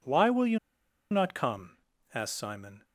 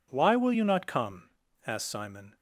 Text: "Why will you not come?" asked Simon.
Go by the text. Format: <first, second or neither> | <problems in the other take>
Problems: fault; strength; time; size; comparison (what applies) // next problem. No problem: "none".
second | pauses between "you" and "not"; noticeable; at 0.5 s; 0.53 s long